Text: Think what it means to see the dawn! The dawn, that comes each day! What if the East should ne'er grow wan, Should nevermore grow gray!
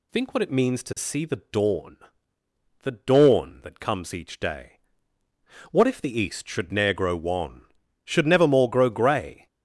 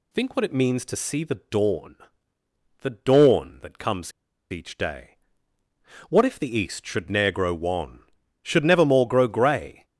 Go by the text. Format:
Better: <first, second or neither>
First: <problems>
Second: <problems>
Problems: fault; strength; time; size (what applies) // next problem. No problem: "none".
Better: first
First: none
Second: pauses between "comes" and "each"; at 4.1 s; 0.39 s long